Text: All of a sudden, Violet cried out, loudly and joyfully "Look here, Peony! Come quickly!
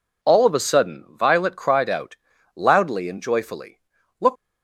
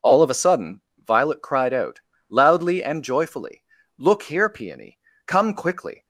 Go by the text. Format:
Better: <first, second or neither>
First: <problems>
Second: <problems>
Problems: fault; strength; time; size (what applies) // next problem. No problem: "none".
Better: second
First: pauses between "joyfully" and "Look"; at 3.7 s; 0.40 s long // stops before "here Peony Come quickly"; at 4.3 s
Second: pauses between "joyfully" and "Look"; slight; at 3.6 s; 0.34 s long